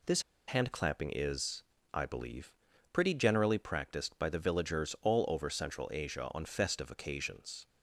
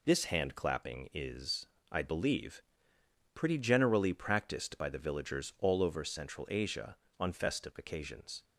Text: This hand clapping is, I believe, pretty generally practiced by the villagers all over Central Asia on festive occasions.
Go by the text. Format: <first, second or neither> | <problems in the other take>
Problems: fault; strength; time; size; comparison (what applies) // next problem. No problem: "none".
second | pauses between "This" and "hand"; slight; at 0.2 s; 0.26 s long